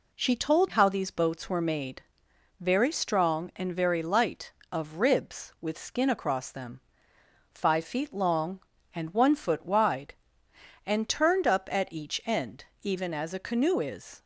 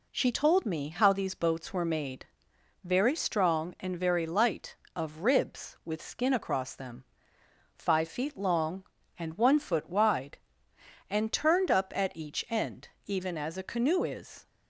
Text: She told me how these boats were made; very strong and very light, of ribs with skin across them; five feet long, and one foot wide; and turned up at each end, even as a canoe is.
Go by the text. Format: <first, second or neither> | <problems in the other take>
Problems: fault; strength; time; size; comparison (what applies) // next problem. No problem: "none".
second | skips "me"; at 0.6 s